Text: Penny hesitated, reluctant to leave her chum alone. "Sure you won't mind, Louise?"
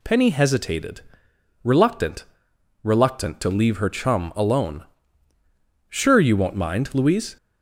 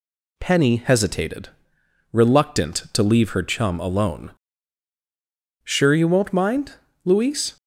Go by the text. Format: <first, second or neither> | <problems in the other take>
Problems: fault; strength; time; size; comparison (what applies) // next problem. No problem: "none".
second | says "reluctant" twice; at 2.8 s